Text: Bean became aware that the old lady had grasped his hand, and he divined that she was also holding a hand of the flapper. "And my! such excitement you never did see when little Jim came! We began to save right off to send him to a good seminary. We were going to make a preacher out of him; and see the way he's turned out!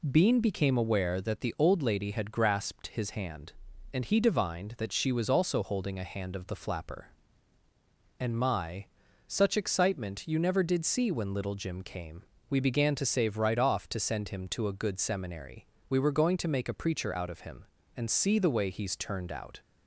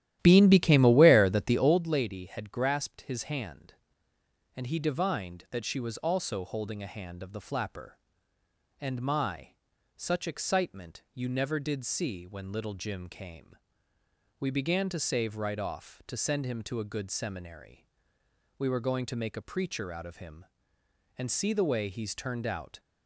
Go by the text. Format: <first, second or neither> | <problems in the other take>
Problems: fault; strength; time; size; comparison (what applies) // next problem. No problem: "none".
first | starts louder than the rest; strong; until 1.9 s; 12.5 dB